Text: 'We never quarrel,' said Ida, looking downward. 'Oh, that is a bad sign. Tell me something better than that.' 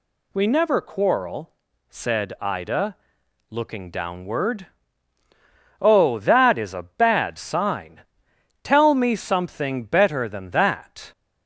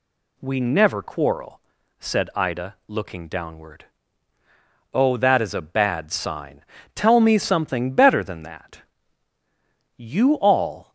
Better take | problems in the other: first | goes on to say "You all"; noticeable; from 9.9 s on; 0.96 s long

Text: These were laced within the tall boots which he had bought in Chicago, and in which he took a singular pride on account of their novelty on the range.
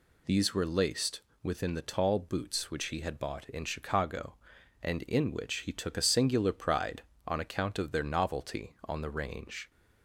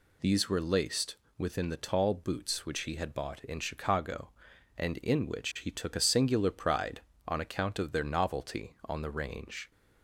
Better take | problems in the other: neither | pauses between "laced" and "within"; slight; the same in both

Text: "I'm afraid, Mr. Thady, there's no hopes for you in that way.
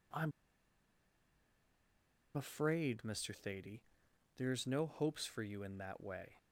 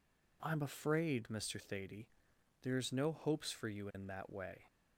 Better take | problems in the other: second | pauses between "I'm" and "afraid"; strong; at 0.3 s; 2.0 s long

